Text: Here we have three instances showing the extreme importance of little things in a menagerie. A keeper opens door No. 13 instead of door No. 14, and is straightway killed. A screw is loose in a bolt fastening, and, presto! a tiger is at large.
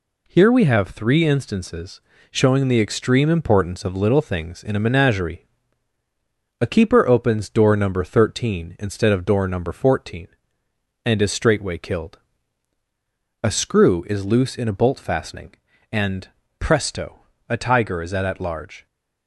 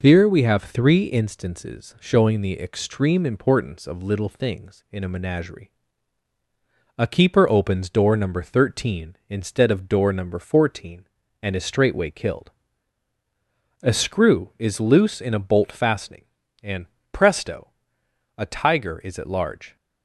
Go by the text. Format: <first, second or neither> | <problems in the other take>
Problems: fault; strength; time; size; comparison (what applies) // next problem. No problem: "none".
second | pauses between "instances" and "showing"; slight; at 1.9 s; 0.30 s long // says "at" twice; at 18.2 s